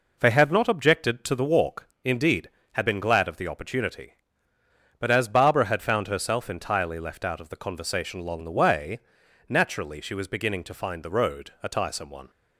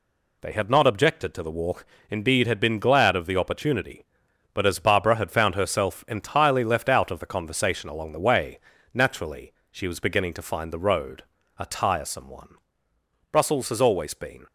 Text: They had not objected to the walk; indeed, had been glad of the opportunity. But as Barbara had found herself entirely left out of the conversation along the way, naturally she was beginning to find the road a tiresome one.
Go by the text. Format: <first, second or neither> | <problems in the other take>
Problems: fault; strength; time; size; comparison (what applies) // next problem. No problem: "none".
first | pauses between "naturally" and "she"; slight; at 9.5 s; 0.18 s long // pauses between "road" and "a"; slight; at 11.2 s; 0.36 s long // goes on to say "Brussels has always been"; noticeable; from 13.3 s on; 1.1 s long